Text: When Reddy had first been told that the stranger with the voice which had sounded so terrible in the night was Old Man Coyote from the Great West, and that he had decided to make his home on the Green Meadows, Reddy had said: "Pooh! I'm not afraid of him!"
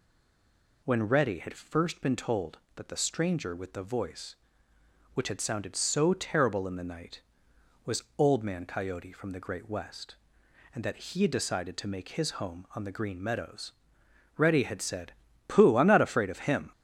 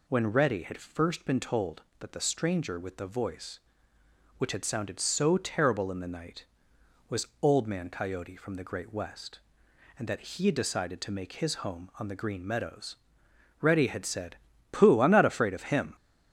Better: second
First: stays silent before the first word; slight; until 0.8 s; 0.8 s long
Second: none

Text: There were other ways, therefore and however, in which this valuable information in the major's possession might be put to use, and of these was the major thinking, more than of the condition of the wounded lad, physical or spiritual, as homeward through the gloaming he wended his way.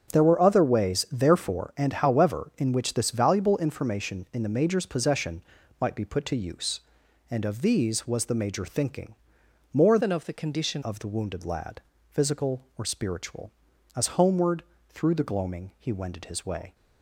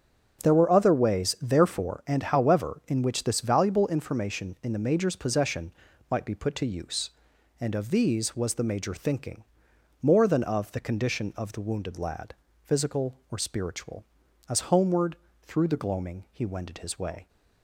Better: second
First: starts louder than the rest; strong; until 1.1 s; 7.5 dB // pauses between "possession" and "might"; slight; at 5.4 s; 0.36 s long // changes voice from "than" to "condition"; from 9.9 to 10.8 s; 0.9 s long // pauses between "homeward" and "through"; slight; at 14.6 s; 0.26 s long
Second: starts louder than the rest; strong; until 1.5 s; 7 dB // pauses between "possession" and "might"; slight; at 5.7 s; 0.36 s long // pauses between "homeward" and "through"; slight; at 15.1 s; 0.26 s long

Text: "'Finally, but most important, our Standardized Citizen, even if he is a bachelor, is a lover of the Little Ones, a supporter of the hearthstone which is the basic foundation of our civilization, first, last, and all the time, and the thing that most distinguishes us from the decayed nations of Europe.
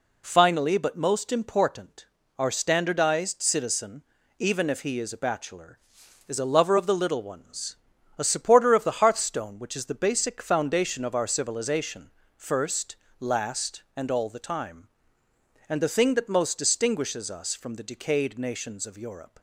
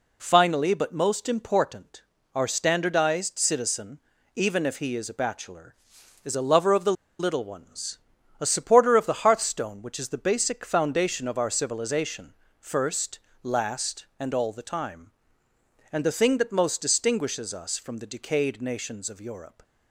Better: first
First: none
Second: pauses between "the" and "Little"; slight; at 6.9 s; 0.26 s long

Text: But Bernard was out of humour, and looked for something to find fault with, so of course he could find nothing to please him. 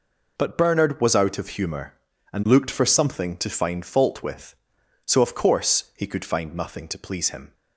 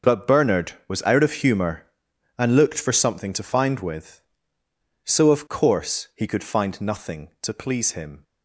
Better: first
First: none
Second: starts louder than the rest; until 1.2 s; 6.5 dB // skips "fault"; at 3.7 s

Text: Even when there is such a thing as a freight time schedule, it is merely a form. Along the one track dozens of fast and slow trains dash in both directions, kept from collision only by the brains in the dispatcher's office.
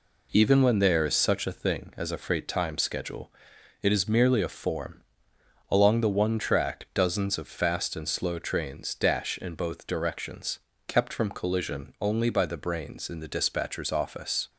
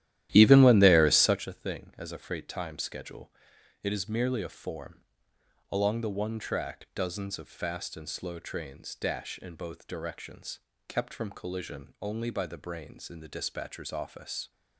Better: first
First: none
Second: starts louder than the rest; strong; until 1.5 s; 13 dB

